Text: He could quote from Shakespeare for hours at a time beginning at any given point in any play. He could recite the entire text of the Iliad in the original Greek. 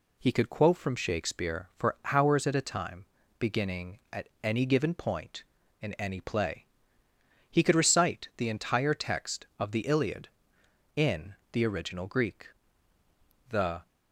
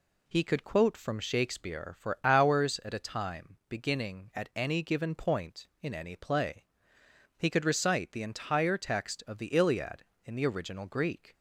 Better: second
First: pauses between "for" and "hours"; slight; at 1.9 s; 0.16 s long // pauses between "time" and "beginning"; slight; at 3.0 s; 0.34 s long // pauses between "in" and "the"; slight; at 11.3 s; 0.18 s long // goes on to say "The"; slight; from 13.4 s on; 0.38 s long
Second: none

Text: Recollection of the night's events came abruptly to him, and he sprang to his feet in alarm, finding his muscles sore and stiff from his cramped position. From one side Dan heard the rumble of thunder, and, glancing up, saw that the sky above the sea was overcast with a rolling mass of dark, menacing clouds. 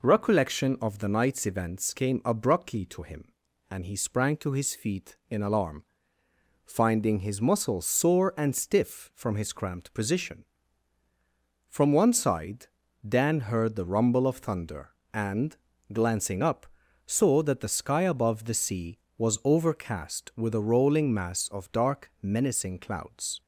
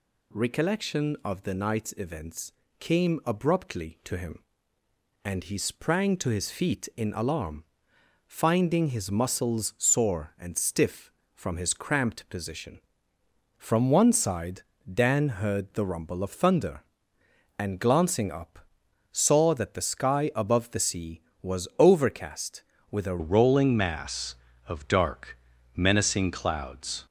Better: first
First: pauses between "side" and "Dan"; at 12.6 s; 0.40 s long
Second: pauses between "events" and "came"; slight; at 2.5 s; 0.26 s long // pauses between "side" and "Dan"; slight; at 14.6 s; 0.30 s long // changes voice at "rolling"; from 23.1 s on; 3.9 s long

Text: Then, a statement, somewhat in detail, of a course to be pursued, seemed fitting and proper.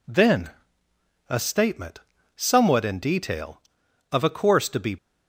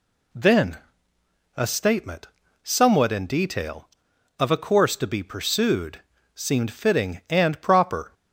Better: second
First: stops before "pursued seemed fitting and proper"; at 4.9 s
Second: none

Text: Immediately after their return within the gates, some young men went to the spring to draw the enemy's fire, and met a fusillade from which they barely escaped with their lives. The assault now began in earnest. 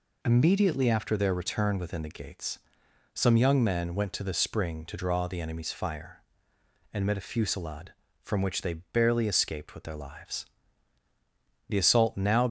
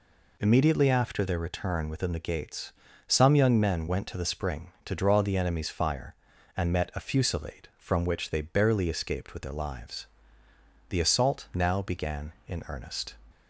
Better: second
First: stops before "began in earnest"; at 12.4 s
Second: none

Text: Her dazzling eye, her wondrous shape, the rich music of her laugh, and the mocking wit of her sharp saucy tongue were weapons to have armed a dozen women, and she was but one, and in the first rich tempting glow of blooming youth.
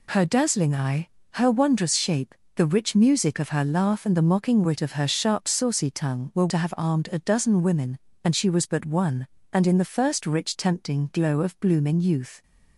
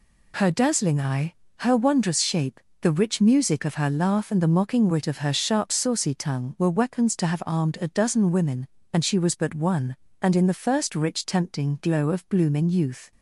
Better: second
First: skips "weapons"; at 6.4 s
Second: none

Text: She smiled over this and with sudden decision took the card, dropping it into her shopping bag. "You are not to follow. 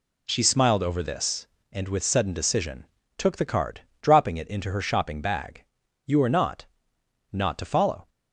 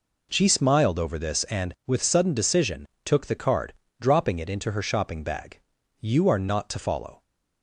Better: second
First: pauses between "decision" and "took"; slight; at 2.8 s; 0.30 s long // says "not" twice; at 7.3 s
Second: pauses between "decision" and "took"; slight; at 2.8 s; 0.18 s long

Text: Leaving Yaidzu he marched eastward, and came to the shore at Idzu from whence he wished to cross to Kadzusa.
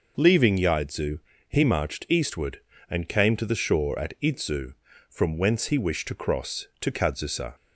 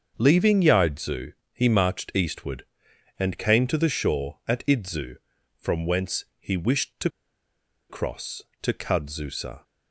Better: first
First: pauses between "Yaidzu" and "he"; slight; at 1.1 s; 0.28 s long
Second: starts louder than the rest; until 1.1 s; 6.5 dB // pauses between "Yaidzu" and "he"; slight; at 1.3 s; 0.20 s long // pauses between "to" and "cross"; noticeable; at 7.1 s; 0.79 s long

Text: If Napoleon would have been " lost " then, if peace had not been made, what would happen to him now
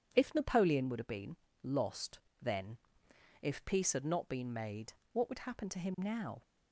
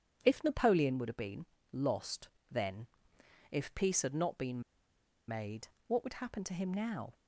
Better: first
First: starts louder than the rest; strong; until 1.1 s; 8 dB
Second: starts louder than the rest; strong; until 1.2 s; 8 dB // pauses between "been" and "made"; noticeable; at 4.6 s; 0.67 s long

